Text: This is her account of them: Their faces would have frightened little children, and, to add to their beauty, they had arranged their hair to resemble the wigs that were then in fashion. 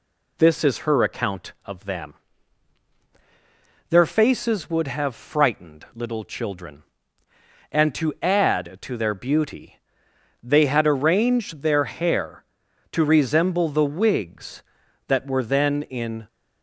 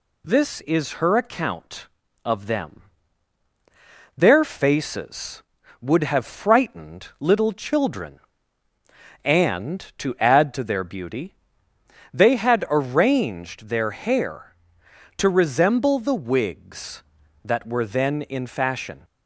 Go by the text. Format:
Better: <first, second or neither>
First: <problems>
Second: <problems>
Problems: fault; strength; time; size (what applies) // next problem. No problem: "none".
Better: second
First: stops before "fashion"; at 16.2 s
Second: none